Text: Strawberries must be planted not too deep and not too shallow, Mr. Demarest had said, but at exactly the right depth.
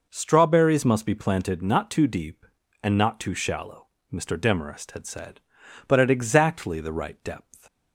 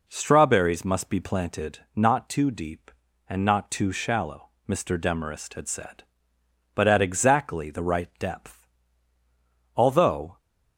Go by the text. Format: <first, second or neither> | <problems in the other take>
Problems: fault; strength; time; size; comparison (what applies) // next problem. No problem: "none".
first | pauses between "planted" and "not"; slight; at 1.7 s; 0.16 s long // goes on to say "Although"; noticeable; from 9.7 s on; 0.62 s long